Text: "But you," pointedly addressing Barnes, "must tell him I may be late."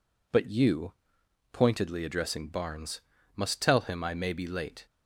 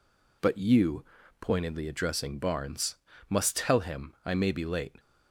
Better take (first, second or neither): neither